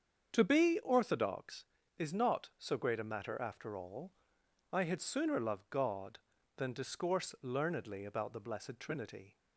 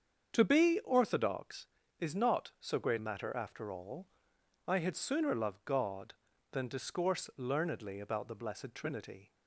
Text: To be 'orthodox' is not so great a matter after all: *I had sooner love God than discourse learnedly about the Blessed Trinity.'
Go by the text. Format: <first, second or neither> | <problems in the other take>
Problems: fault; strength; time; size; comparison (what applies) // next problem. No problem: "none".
first | starts louder than the rest; strong; until 1.3 s; 7.5 dB; strong in the first // skips "a"; at 2.9 s